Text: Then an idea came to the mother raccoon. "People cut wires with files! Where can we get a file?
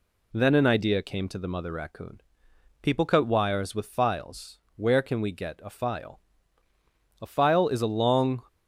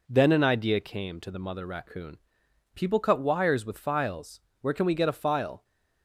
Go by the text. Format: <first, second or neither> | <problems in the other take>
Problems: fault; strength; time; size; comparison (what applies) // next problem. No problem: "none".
second | goes on to say "A file is a long"; noticeable; from 7.1 s on; 1.2 s long